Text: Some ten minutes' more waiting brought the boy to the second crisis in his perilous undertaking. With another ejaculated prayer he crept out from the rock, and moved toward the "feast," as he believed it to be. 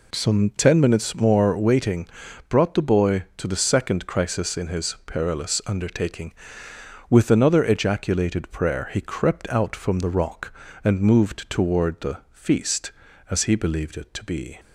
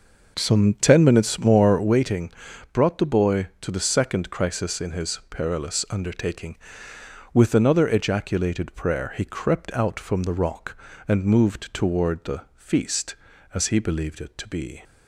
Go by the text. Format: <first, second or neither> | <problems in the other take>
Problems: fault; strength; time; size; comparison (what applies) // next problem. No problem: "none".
first | starts louder than the rest; noticeable; until 2.0 s; 5.5 dB // pauses between "waiting" and "brought"; at 2.3 s; 0.40 s long; also in the first